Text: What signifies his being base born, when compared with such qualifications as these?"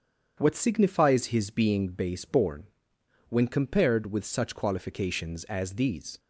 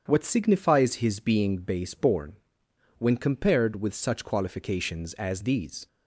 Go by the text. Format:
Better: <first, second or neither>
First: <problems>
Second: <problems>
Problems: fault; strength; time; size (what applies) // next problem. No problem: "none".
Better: neither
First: starts louder than the rest; strong; until 1.4 s; 8 dB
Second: starts louder than the rest; strong; until 1.0 s; 8 dB